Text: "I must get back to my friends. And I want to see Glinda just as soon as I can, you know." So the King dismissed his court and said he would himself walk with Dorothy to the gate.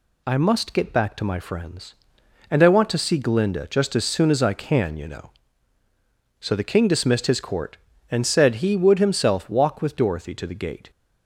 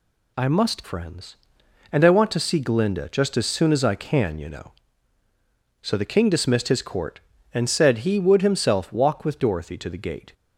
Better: first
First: none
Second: skips "get back to my"; at 0.8 s

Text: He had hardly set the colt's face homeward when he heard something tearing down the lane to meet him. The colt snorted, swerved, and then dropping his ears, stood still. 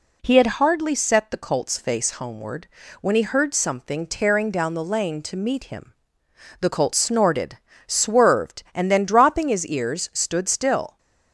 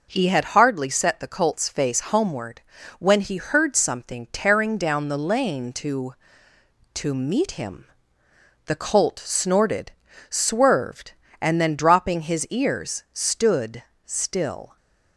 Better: first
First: pauses between "homeward" and "when"; slight; at 2.6 s; 0.32 s long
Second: pauses between "homeward" and "when"; slight; at 2.6 s; 0.36 s long // says "to" twice; at 6.9 s // pauses between "stood" and "still"; slight; at 13.8 s; 0.22 s long

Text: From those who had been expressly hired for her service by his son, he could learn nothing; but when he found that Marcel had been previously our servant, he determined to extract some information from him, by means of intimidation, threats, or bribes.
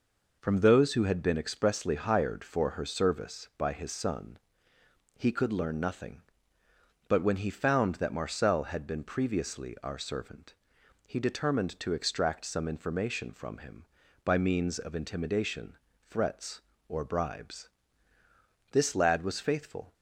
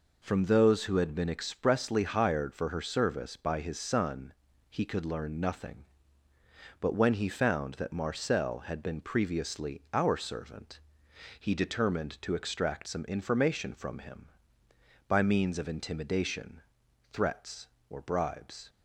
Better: second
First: goes on to say "This lad was faithful"; noticeable; from 18.6 s on; 1.2 s long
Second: none

